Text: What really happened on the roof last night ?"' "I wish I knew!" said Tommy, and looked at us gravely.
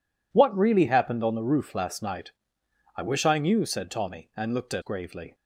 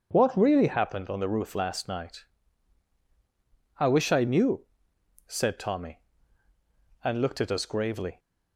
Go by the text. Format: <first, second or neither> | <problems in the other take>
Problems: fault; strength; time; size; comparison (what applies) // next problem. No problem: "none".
second | skips "us"; at 4.8 s